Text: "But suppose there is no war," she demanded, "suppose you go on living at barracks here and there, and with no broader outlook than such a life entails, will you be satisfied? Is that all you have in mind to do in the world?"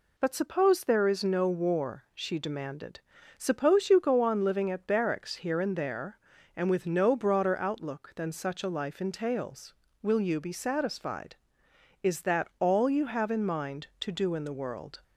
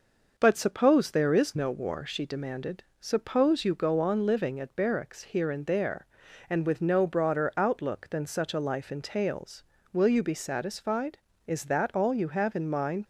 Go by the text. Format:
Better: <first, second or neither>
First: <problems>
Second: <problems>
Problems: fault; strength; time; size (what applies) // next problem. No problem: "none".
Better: first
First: none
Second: stops before "to do in the world"; at 13.0 s